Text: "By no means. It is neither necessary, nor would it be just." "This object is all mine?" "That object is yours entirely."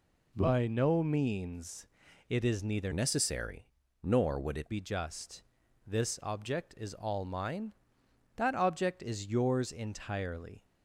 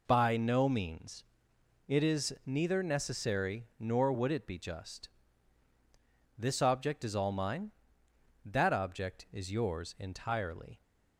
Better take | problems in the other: second | changes voice from "necessary" to "it"; from 2.9 to 4.7 s; 1.8 s long

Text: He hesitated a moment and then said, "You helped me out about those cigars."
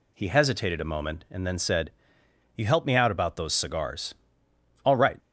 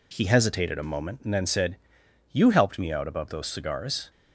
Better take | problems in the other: second | goes on to say "All right"; slight; from 4.8 s on; 0.34 s long

